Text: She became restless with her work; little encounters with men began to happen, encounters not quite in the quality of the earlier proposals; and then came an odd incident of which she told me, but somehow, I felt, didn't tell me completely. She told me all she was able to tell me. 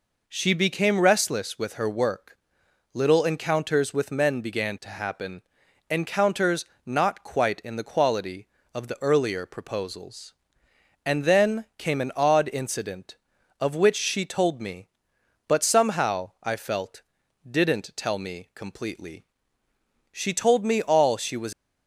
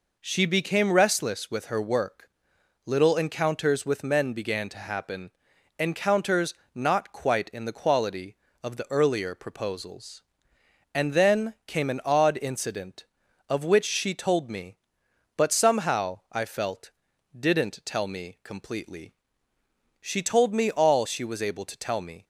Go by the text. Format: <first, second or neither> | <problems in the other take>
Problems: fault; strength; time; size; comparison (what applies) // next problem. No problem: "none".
second | pauses between "encounters" and "not"; slight; at 6.6 s; 0.20 s long; slight in the second // stops before "able to tell me"; at 21.5 s